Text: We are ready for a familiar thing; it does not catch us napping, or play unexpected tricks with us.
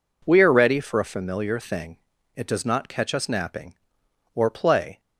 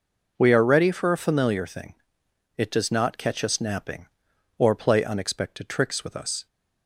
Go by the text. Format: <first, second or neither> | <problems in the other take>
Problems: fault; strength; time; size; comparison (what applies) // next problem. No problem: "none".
second | stops before "unexpected tricks with us"; at 4.9 s